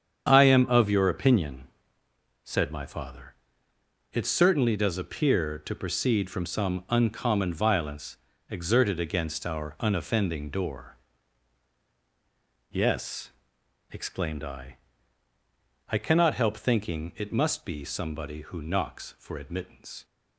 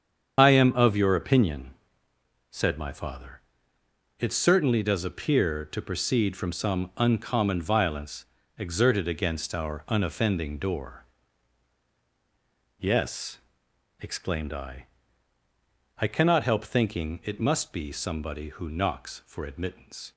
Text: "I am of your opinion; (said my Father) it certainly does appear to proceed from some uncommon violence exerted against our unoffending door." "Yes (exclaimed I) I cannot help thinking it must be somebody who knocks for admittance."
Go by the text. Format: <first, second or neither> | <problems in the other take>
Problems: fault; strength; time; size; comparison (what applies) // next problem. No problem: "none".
first | loses the start of "I"; at 0.3 s; 50 ms // starts louder than the rest; strong; until 1.3 s; 8 dB; strong in the first // pauses between "violence" and "exerted"; slight; at 8.2 s; 0.34 s long; slight in the first